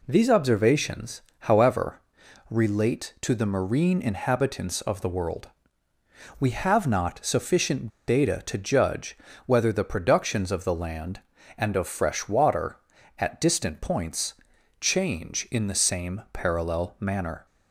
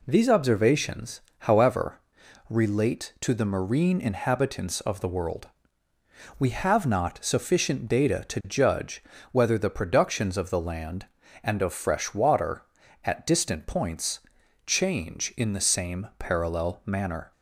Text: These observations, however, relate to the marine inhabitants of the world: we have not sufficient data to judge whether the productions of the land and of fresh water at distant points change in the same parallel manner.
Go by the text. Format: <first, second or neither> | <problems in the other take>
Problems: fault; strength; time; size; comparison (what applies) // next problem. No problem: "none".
second | pauses between "sufficient" and "data"; slight; at 7.8 s; 0.19 s long // pauses between "judge" and "whether"; slight; at 9.1 s; 0.28 s long; slight in the second // pauses between "points" and "change"; noticeable; at 14.3 s; 0.48 s long; noticeable in the second